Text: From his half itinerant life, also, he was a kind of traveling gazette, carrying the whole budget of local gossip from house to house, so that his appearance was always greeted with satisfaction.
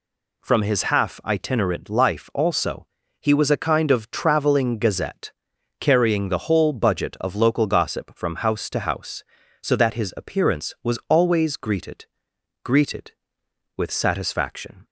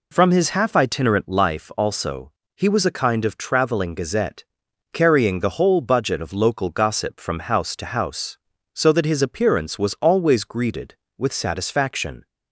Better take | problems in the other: second | says "greeted" twice; at 12.6 s

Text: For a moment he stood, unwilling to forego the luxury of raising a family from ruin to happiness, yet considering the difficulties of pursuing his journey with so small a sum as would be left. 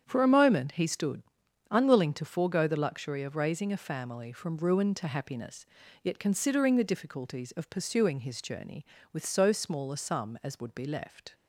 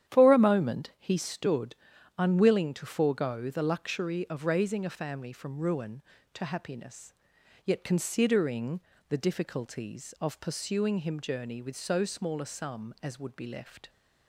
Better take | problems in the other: first | starts louder than the rest; strong; until 1.1 s; 10 dB; strong in the first // pauses between "considering" and "the"; slight; at 8.7 s; 0.30 s long // says "him" for "his"; at 10.9 s

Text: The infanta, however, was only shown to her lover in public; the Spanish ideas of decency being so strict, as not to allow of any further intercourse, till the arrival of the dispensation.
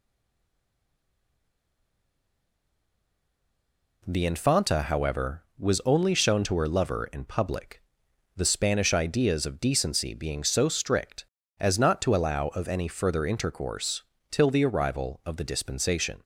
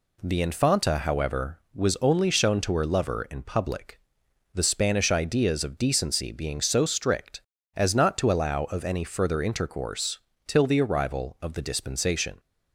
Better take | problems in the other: second | stays silent before the first word; strong; until 4.0 s; 4.0 s long

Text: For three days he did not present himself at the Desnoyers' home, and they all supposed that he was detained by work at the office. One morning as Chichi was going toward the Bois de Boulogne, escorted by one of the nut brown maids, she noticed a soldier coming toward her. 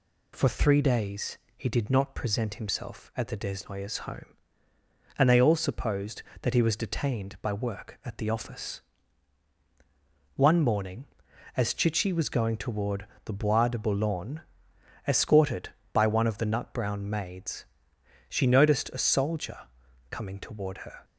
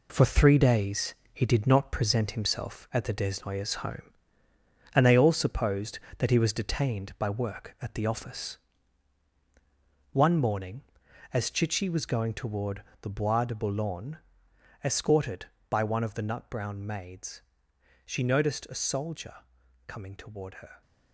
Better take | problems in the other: first | gets quieter; throughout; 7 dB // pauses between "days" and "he"; slight; at 1.1 s; 0.18 s long; slight in the first // pauses between "toward" and "the"; slight; at 12.8 s; 0.20 s long; slight in the first // pauses between "soldier" and "coming"; noticeable; at 19.3 s; 0.52 s long; noticeable in the first

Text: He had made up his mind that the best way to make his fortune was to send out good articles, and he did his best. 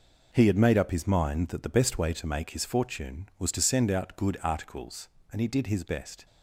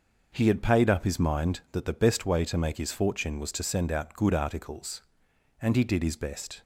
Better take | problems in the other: first | says "paid" for "made"; at 0.6 s

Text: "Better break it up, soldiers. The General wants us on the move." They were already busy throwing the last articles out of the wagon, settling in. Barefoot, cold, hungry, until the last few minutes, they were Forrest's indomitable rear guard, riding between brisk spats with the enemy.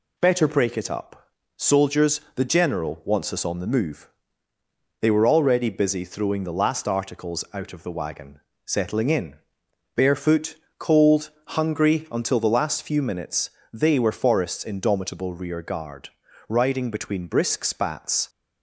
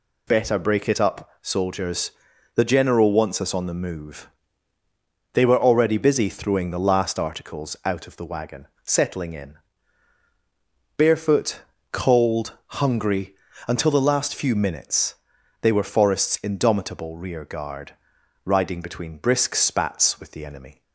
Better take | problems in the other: second | stops before "with the enemy"; at 18.2 s

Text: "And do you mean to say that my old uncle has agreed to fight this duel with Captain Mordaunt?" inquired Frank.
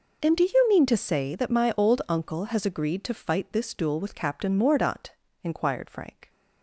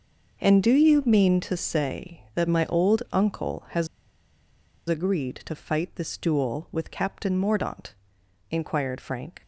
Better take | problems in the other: first | pauses between "has" and "agreed"; at 3.8 s; 1.0 s long

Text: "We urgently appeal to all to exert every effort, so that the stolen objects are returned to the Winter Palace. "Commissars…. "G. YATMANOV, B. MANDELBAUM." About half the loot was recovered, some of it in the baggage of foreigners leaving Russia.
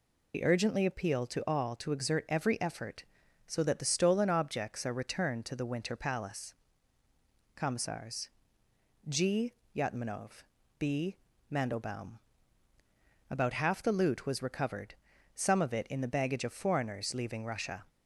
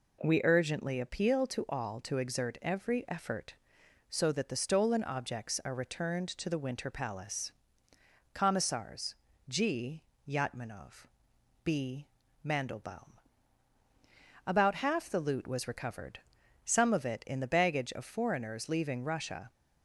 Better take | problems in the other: second | loses the start of "We"; at 0.3 s; 65 ms

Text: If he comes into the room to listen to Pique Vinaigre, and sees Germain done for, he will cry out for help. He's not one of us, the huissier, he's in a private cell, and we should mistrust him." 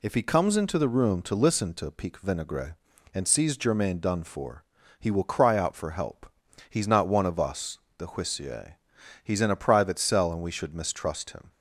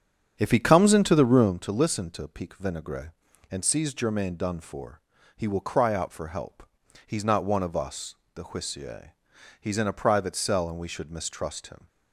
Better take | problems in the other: first | starts louder than the rest; strong; until 1.5 s; 8 dB

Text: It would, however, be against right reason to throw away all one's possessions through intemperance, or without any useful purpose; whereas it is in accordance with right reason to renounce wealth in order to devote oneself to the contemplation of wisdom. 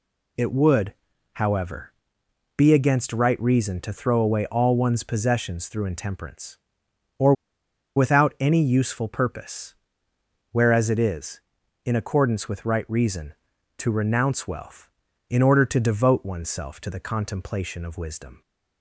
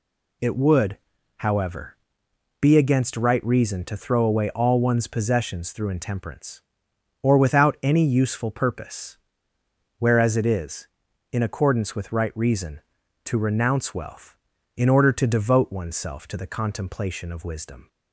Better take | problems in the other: second | pauses between "or" and "without"; noticeable; at 7.3 s; 0.62 s long

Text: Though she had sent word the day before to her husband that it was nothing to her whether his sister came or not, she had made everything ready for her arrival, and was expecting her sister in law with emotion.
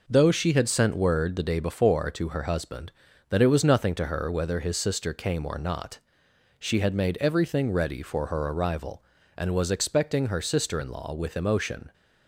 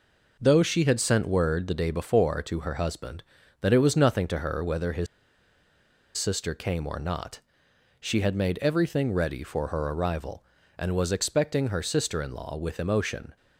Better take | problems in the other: first | pauses between "his" and "sister"; at 5.0 s; 1.1 s long

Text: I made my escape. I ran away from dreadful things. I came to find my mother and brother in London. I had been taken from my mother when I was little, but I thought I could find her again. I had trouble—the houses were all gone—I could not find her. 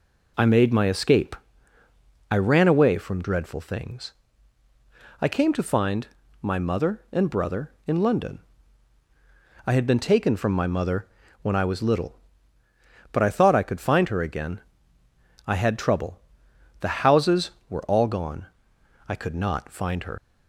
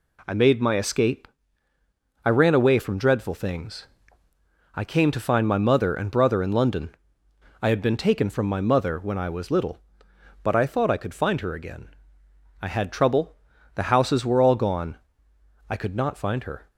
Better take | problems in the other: second | pauses between "find" and "my"; slight; at 6.0 s; 0.34 s long // pauses between "mother" and "when"; slight; at 11.0 s; 0.36 s long // leaves "her" unfinished; at 20.1 s; 120 ms

